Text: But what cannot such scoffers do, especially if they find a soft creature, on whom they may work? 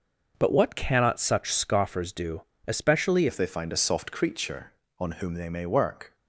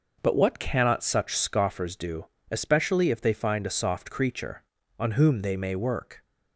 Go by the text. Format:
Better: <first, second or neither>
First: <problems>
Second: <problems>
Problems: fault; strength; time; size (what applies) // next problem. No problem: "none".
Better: second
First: starts louder than the rest; until 1.3 s; 6 dB // changes voice at "if"; from 3.2 s on; 2.9 s long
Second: none